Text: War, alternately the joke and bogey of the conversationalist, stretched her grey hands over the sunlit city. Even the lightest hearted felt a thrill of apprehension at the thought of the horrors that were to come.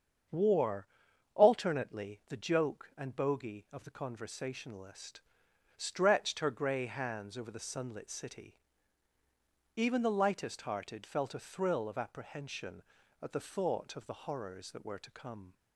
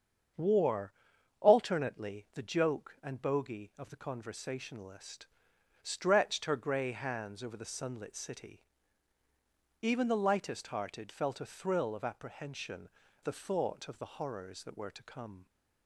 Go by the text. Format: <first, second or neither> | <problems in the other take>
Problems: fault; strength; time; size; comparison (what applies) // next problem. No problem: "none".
first | starts louder than the rest; strong; until 1.8 s; 7.5 dB; strong in the first // skips "at"; at 13.0 s